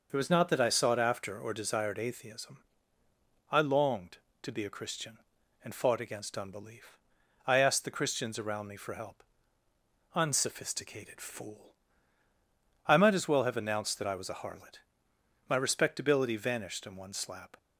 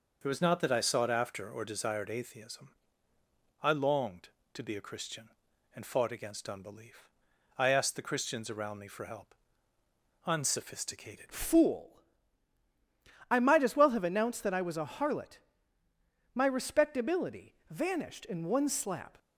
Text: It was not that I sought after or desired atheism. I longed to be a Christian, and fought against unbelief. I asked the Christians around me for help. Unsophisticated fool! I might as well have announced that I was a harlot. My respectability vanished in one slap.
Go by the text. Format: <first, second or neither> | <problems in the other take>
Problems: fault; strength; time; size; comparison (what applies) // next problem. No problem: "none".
first | changes voice at "fool"; from 11.2 s on; 7.9 s long // pauses between "respectability" and "vanished"; slight; at 17.5 s; 0.16 s long